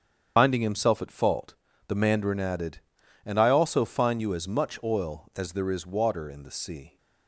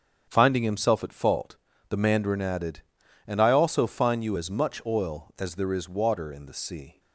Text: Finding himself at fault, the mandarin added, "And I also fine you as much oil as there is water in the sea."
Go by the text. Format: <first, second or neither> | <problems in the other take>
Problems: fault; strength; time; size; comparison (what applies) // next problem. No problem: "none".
second | loses the start of "Finding"; at 0.3 s; 95 ms // starts louder than the rest; strong; until 1.3 s; 8 dB; strong in the second